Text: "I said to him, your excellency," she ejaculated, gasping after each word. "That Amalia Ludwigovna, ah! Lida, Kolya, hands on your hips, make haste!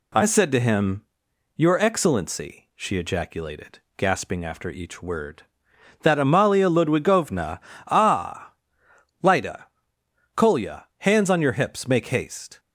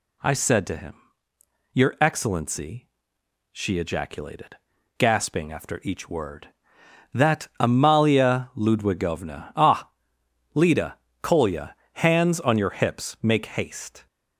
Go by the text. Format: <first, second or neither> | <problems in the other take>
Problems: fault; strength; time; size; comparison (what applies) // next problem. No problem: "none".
neither | none